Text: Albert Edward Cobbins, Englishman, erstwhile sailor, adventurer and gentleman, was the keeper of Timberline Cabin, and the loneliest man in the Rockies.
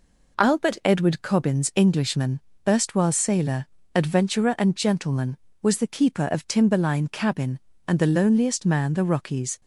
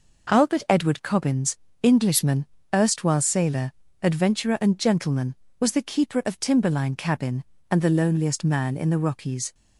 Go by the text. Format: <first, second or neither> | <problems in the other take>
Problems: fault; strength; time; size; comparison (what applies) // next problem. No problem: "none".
second | skips "in"; at 8.9 s